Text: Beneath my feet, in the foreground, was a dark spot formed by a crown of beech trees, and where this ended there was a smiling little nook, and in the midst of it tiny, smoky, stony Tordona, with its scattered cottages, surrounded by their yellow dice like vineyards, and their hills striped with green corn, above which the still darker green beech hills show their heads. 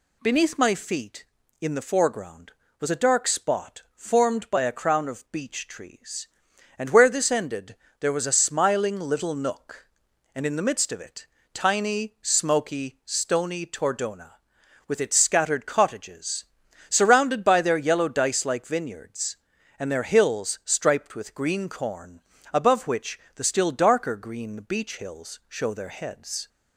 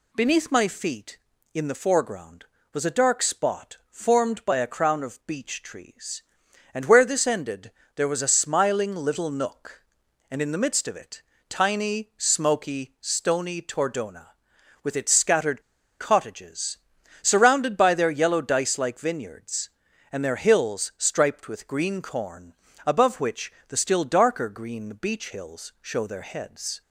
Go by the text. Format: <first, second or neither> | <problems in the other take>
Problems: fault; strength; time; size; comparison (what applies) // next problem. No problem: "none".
first | pauses between "ended" and "there"; slight; at 7.7 s; 0.24 s long; slight in the first // pauses between "it" and "tiny"; slight; at 11.2 s; 0.26 s long; slight in the first // pauses between "scattered" and "cottages"; at 15.6 s; 0.37 s long